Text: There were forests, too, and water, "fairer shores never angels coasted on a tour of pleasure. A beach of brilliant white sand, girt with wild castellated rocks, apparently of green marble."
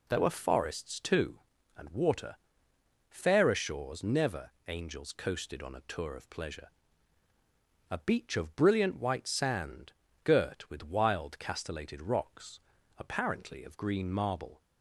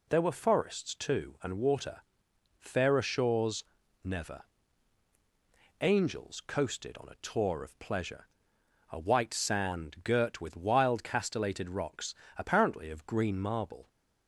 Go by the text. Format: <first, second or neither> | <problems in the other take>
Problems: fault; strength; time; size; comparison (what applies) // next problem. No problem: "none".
first | pauses between "shores" and "never"; at 3.6 s; 0.40 s long // pauses between "never" and "angels"; strong; at 4.4 s; 1.3 s long; slight in the first // skips "beach of brilliant"; at 8.9 s